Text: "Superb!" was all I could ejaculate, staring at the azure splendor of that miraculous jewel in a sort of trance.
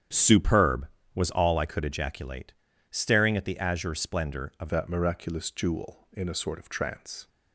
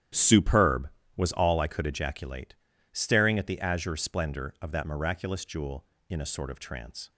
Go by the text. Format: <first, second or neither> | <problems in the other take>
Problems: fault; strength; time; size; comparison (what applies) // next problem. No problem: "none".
second | starts louder than the rest; strong; until 1.4 s; 9 dB; strong in the second // changes voice at "that"; from 4.7 s on; 2.5 s long